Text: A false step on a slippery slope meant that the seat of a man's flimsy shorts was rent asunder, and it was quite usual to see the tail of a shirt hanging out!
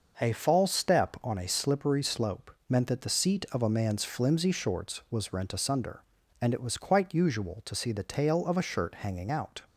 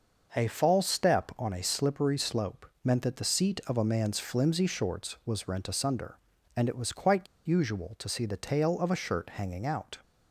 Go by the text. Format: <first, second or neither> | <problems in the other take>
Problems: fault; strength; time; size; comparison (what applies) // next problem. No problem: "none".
first | pauses between "slope" and "meant"; slight; at 2.6 s; 0.20 s long; slight in the first // pauses between "quite" and "usual"; slight; at 7.2 s; 0.20 s long